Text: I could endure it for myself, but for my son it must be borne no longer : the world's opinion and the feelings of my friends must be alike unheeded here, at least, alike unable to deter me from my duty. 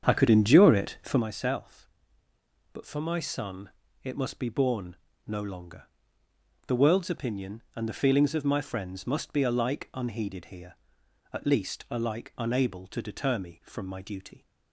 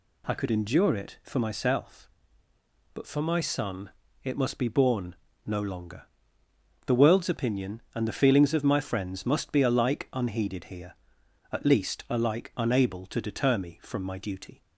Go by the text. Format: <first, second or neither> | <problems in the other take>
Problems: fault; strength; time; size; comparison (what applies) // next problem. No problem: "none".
second | starts louder than the rest; strong; until 1.2 s; 8 dB // pauses between "son" and "it"; slight; at 3.7 s; 0.32 s long; slight in the second // pauses between "borne" and "no"; slight; at 4.9 s; 0.30 s long; slight in the second